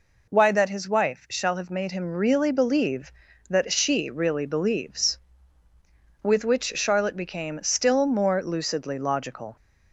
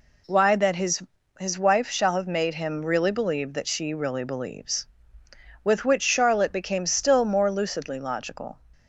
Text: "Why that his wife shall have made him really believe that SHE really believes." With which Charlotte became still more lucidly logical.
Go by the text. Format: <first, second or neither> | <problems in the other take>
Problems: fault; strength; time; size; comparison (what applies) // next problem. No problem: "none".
first | says "his" twice; at 1.3 s